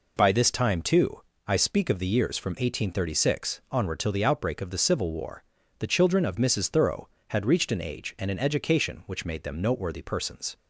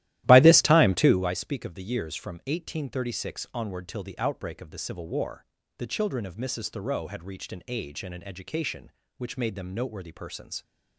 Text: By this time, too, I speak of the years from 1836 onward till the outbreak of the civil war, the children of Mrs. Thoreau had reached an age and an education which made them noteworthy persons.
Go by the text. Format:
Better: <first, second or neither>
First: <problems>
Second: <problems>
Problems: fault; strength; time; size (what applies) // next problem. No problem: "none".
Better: first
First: none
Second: starts louder than the rest; strong; until 1.3 s; 14.5 dB